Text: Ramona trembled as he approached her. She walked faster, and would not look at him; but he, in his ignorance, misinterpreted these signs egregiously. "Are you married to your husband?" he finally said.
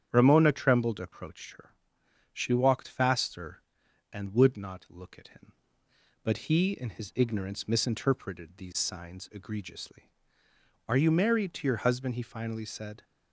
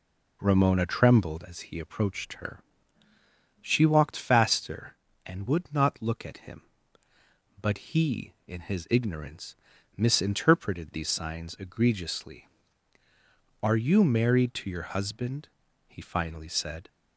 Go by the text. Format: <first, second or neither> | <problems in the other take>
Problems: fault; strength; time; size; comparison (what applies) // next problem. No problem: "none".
second | starts louder than the rest; strong; until 1.1 s; 9 dB // skips "as he"; at 0.9 s